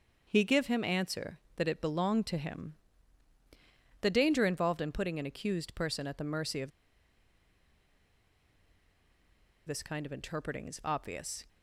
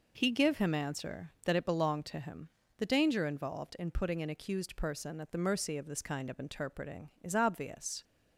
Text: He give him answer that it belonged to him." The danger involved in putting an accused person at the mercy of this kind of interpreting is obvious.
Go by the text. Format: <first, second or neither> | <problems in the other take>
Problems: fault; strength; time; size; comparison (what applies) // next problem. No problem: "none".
second | starts louder than the rest; until 1.2 s; 6.5 dB // pauses between "of" and "this"; strong; at 6.7 s; 2.9 s long